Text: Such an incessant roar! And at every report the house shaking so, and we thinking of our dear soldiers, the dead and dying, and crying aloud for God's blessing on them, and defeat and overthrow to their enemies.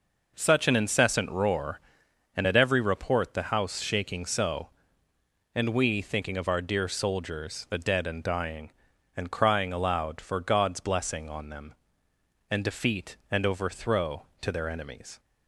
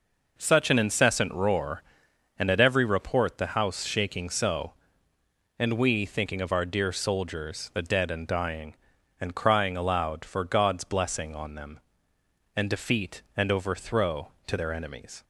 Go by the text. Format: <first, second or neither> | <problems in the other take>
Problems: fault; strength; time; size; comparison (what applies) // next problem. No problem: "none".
neither | none